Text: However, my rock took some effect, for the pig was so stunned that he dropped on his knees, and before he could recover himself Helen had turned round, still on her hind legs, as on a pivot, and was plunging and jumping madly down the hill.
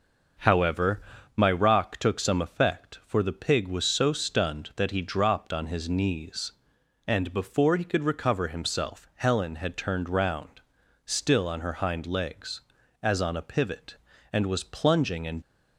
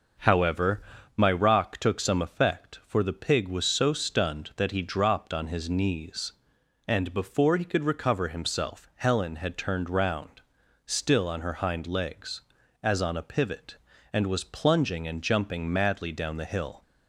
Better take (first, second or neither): second